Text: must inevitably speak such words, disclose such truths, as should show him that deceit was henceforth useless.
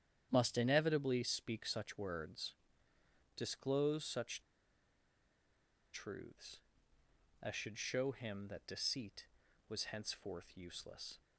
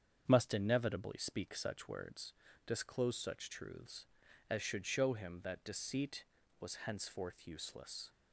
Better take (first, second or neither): second